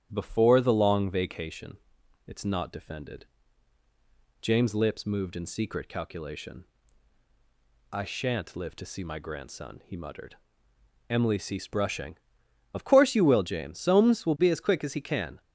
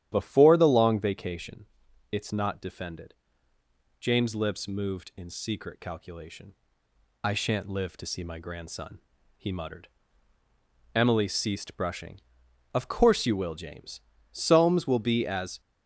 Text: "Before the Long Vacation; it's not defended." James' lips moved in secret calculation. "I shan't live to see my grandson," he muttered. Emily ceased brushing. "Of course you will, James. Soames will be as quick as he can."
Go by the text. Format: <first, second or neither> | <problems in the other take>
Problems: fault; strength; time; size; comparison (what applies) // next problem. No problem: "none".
first | starts louder than the rest; strong; until 1.1 s; 11 dB; strong in the first // stops before "quick as he can"; at 15.6 s